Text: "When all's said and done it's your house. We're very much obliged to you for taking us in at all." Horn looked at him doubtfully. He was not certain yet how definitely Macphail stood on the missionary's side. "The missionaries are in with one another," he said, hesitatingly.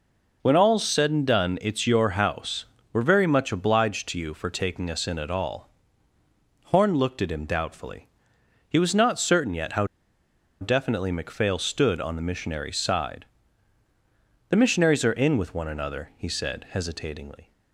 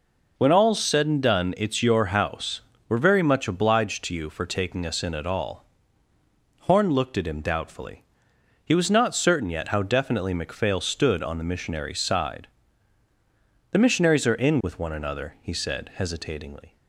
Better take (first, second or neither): second